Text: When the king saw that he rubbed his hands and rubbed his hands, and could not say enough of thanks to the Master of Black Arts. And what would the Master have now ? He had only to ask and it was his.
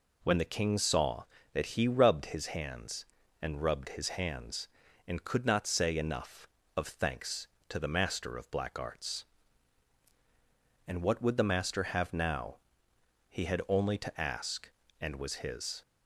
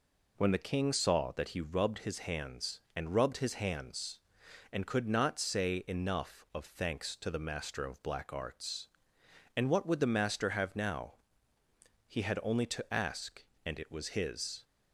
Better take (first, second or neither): second